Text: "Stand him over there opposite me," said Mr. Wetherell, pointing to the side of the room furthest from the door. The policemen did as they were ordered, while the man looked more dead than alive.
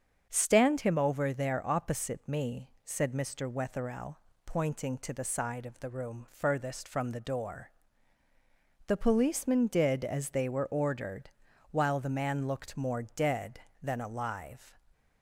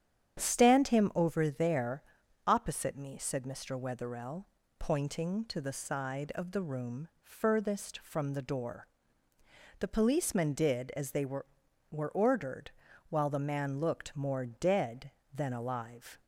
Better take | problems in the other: first | starts louder than the rest; strong; until 1.4 s; 9 dB; also in the first // pauses between "there" and "opposite"; at 2.0 s; 0.42 s long // pauses between "room" and "furthest"; slight; at 7.0 s; 0.16 s long // says "were" twice; at 11.9 s

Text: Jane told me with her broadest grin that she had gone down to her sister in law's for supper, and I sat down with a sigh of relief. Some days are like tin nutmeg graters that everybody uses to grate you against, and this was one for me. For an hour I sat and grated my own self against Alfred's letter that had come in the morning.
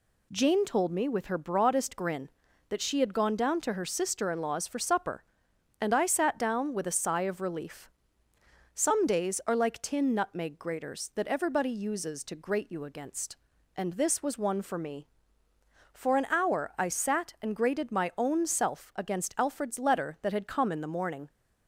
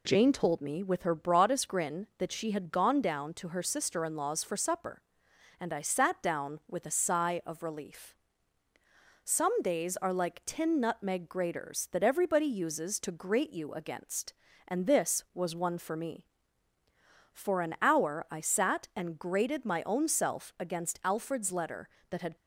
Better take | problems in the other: first | stops before "come in the morning"; at 22.3 s

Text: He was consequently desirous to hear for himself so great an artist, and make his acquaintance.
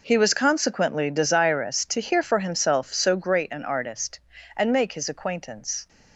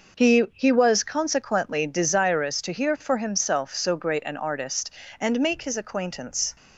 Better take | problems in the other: first | says "He" twice; at 0.5 s

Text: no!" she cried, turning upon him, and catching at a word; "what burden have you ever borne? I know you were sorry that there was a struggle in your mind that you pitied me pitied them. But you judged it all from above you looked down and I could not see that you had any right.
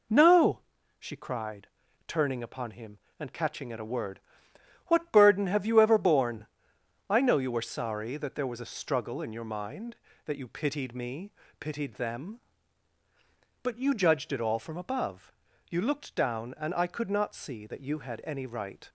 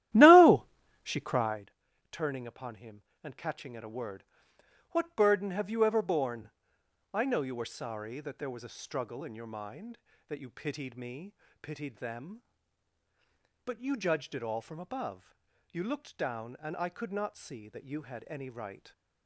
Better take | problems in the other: first | starts louder than the rest; strong; until 1.7 s; 13.5 dB // pauses between "me" and "pitied"; slight; at 11.3 s; 0.30 s long; slight in the first // pauses between "above" and "you"; at 15.3 s; 0.38 s long; also in the first

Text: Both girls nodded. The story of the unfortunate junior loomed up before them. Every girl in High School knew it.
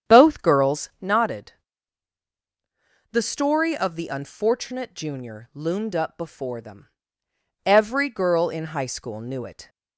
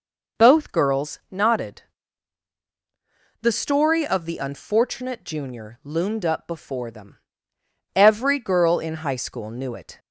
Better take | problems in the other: second | starts louder than the rest; strong; until 1.2 s; 8.5 dB

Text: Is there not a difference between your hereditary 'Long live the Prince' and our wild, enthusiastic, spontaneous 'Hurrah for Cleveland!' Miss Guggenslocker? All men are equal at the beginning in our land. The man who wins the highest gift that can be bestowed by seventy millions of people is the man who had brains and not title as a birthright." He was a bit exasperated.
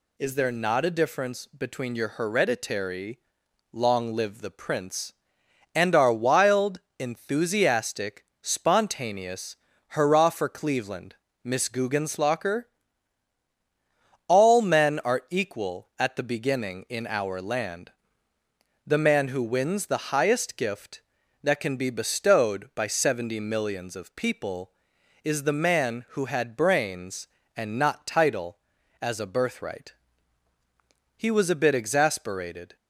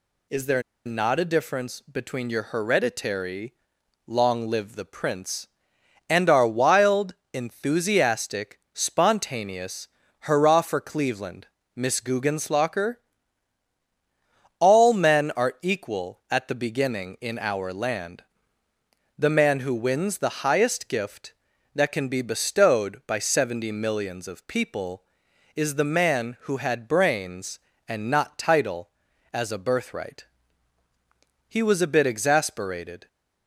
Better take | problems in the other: first | pauses between "there" and "not"; slight; at 0.6 s; 0.23 s long // pauses between "hereditary" and "Long"; noticeable; at 3.5 s; 0.54 s long; noticeable in the first // pauses between "spontaneous" and "Hurrah"; slight; at 9.8 s; 0.34 s long; slight in the first

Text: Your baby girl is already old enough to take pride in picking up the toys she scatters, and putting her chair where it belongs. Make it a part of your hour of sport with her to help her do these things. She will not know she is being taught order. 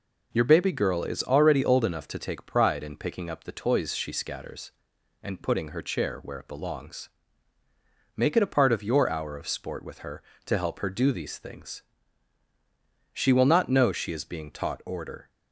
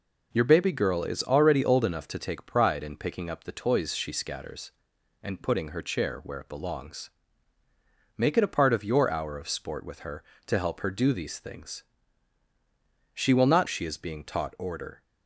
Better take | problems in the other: first | skips "know"; at 13.6 s

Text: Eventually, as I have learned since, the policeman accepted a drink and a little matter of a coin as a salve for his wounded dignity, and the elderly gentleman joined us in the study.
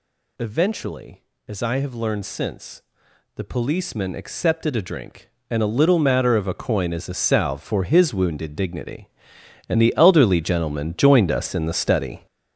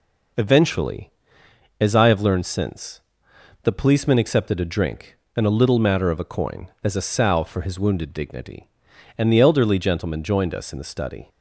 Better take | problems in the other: second | gets louder; strong; throughout; 8.5 dB

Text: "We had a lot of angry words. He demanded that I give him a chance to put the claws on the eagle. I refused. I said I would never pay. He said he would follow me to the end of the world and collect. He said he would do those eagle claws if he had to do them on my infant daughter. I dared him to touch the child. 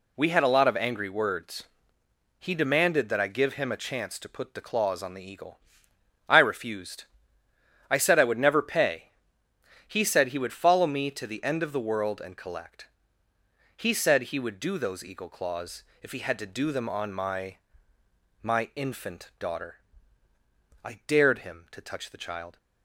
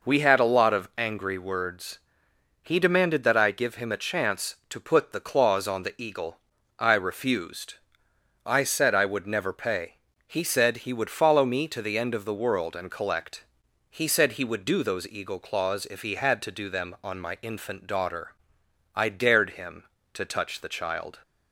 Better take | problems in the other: second | pauses between "claws" and "if"; slight; at 15.8 s; 0.20 s long // says "my" twice; at 18.4 s

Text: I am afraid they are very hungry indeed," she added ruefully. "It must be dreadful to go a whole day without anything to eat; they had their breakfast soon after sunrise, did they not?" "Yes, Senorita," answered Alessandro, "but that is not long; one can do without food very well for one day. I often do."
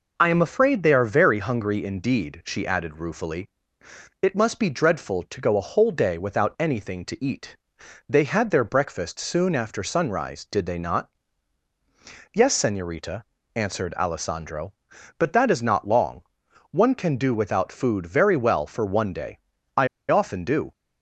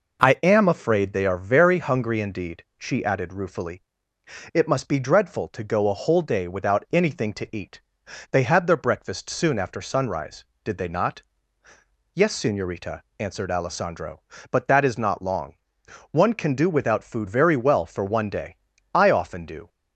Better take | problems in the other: second | pauses between "I" and "often"; slight; at 19.8 s; 0.23 s long

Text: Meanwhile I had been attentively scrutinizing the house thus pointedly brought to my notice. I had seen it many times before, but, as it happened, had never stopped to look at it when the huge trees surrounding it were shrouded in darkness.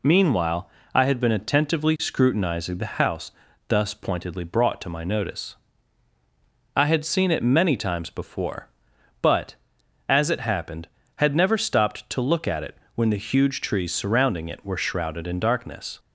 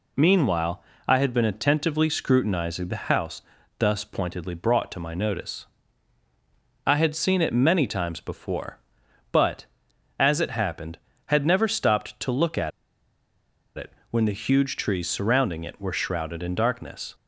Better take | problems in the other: first | pauses between "Meanwhile" and "I"; slight; at 0.8 s; 0.26 s long; slight in the first // pauses between "house" and "thus"; at 3.4 s; 0.38 s long; also in the first // pauses between "at" and "it"; at 12.7 s; 1.0 s long // pauses between "it" and "when"; slight; at 13.9 s; 0.18 s long; slight in the first

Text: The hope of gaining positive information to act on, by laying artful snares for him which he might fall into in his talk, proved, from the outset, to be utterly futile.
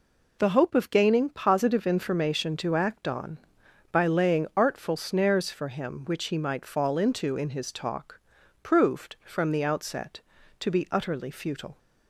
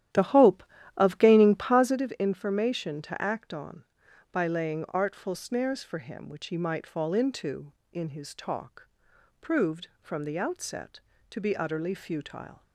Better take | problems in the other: first | starts louder than the rest; strong; until 2.0 s; 12 dB

